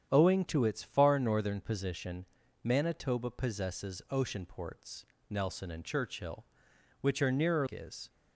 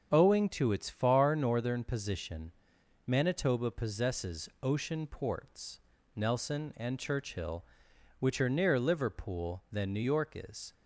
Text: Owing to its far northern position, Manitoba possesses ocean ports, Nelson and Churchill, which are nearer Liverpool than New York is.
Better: second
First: starts louder than the rest; strong; until 1.1 s; 8.5 dB // skips "Liverpool than New York"; at 7.6 s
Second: starts louder than the rest; until 1.1 s; 7 dB

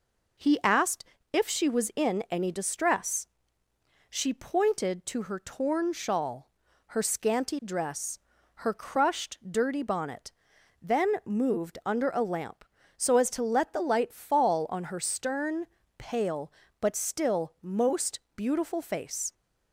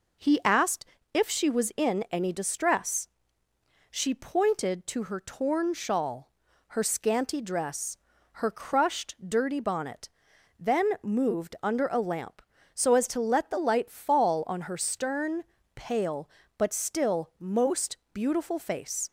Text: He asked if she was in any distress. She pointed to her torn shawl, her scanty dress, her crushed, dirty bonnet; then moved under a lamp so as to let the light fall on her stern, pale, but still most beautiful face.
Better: neither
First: pauses between "asked" and "if"; slight; at 1.0 s; 0.30 s long // pauses between "most" and "beautiful"; slight; at 18.1 s; 0.16 s long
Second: pauses between "asked" and "if"; slight; at 0.8 s; 0.30 s long // pauses between "most" and "beautiful"; slight; at 17.9 s; 0.16 s long

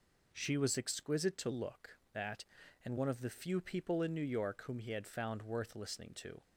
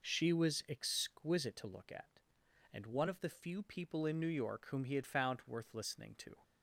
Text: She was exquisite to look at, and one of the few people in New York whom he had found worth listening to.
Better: second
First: says "that" for "at"; at 2.1 s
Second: none

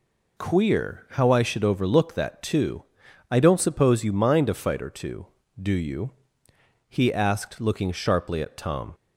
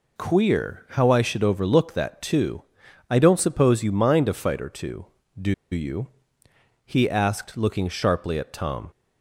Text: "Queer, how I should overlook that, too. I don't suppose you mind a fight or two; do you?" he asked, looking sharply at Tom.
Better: first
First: none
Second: pauses between "do" and "you"; slight; at 5.5 s; 0.19 s long

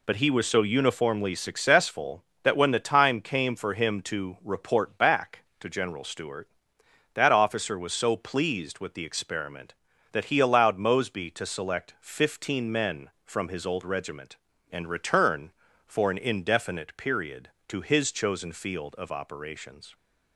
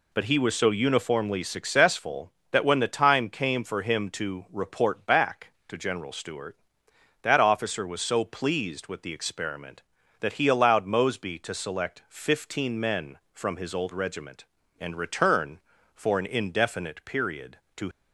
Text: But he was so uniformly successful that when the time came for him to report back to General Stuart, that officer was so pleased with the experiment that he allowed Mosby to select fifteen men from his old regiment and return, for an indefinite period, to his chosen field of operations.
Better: first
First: none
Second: stops before "his chosen field of operations"; at 17.9 s

